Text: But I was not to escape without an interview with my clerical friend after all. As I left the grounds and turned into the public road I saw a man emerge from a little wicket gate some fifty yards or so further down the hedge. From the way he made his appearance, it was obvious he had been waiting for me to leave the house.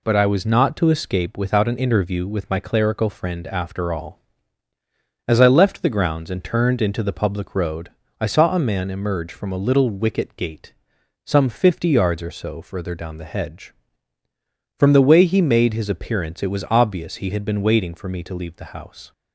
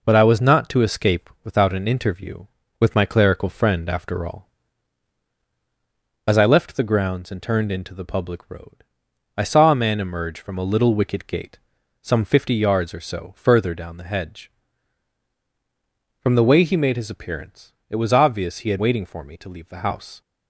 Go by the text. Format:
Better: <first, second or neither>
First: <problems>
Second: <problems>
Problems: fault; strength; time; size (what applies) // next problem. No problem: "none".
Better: first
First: pauses between "road" and "I"; slight; at 7.8 s; 0.30 s long // pauses between "gate" and "some"; noticeable; at 10.7 s; 0.50 s long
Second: pauses between "road" and "I"; noticeable; at 8.8 s; 0.52 s long // pauses between "gate" and "some"; at 11.5 s; 0.44 s long // skips "been"; at 18.7 s